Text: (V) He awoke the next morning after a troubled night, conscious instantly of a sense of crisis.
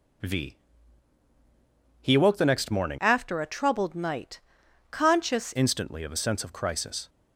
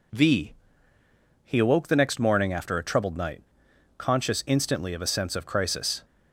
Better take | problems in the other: second | changes voice from "after" to "conscious"; from 2.9 to 5.5 s; 2.6 s long

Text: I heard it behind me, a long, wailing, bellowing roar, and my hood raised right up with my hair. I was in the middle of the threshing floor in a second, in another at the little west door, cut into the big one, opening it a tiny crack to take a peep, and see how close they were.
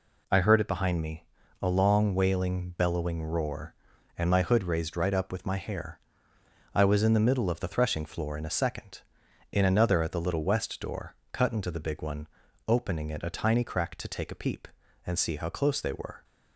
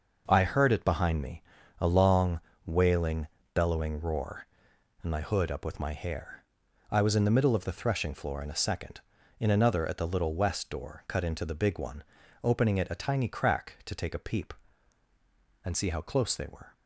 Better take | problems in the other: first | skips "raised right"; at 5.5 s

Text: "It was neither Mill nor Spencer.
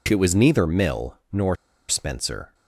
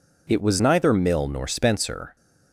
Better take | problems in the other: second | pauses between "Mill" and "nor"; slight; at 1.1 s; 0.16 s long // pauses between "nor" and "Spencer"; slight; at 1.5 s; 0.33 s long

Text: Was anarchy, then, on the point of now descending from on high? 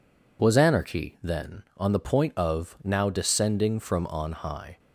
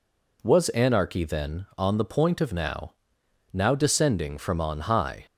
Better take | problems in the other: first | says "now" twice; at 3.5 s

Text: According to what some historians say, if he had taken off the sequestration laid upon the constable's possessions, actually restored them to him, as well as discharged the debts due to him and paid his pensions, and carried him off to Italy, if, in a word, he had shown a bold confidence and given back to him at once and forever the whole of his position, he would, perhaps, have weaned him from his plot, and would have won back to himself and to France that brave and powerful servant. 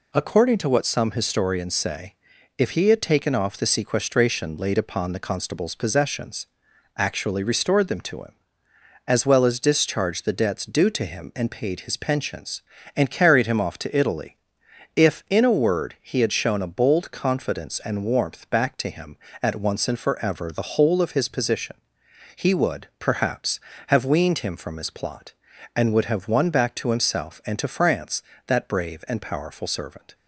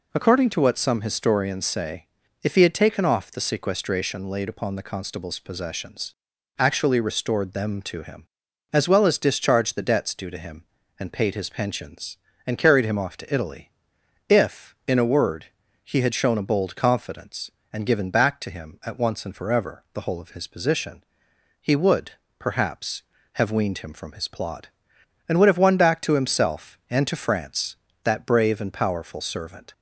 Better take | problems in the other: second | says "warmth" for "given"; at 18.0 s

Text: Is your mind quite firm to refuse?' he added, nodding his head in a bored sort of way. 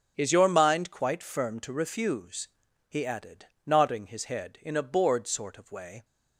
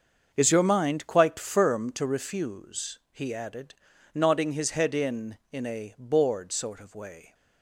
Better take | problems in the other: first | starts louder than the rest; until 1.3 s; 6.5 dB; also in the first // says "in" twice; at 5.5 s

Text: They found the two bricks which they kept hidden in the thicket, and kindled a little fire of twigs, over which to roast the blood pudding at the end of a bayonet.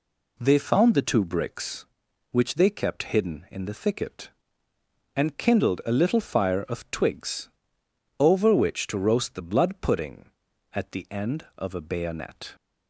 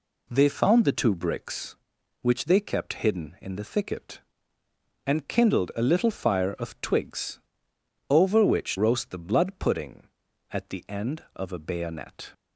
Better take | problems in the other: first | skips "to"; at 8.7 s

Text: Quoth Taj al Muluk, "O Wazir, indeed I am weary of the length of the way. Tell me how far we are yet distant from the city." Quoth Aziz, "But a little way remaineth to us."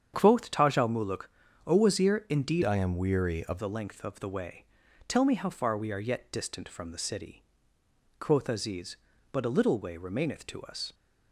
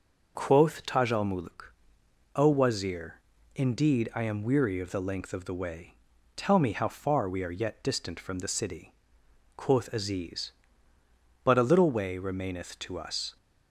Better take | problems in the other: second | starts louder than the rest; strong; until 1.1 s; 8 dB // changes voice from "I" to "of"; from 2.6 to 3.5 s; 0.9 s long

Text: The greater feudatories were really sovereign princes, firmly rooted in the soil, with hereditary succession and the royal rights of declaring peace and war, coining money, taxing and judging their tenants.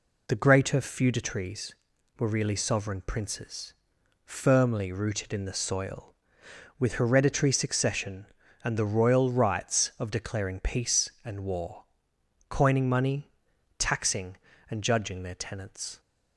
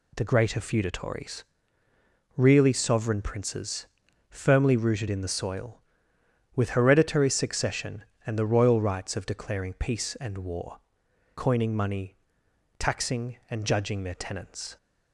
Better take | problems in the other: first | skips "were"; at 1.8 s

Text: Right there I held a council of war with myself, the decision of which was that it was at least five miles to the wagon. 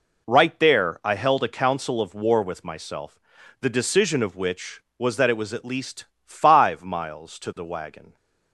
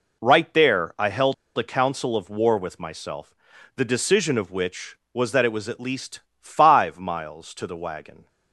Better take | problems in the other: first | pauses between "held" and "a"; slight; at 1.3 s; 0.22 s long // pauses between "least" and "five"; slight; at 6.1 s; 0.20 s long; slight in the first

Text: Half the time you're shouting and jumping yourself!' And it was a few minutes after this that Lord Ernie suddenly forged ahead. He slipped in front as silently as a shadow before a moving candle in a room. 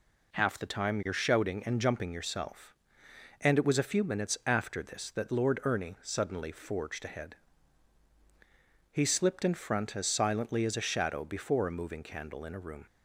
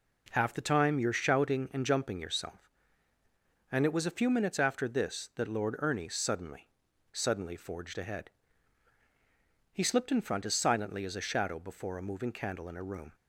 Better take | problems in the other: first | says "suddenly" twice; at 7.1 s

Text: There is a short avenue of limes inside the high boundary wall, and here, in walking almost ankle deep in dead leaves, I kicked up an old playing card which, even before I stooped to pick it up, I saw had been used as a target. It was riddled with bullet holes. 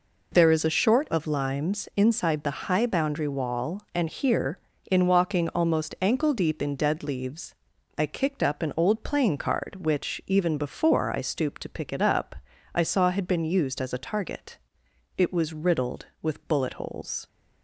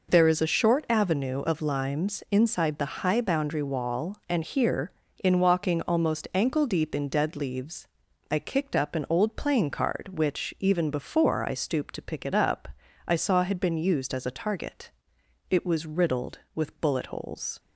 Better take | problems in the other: second | skips "avenue"; at 1.0 s

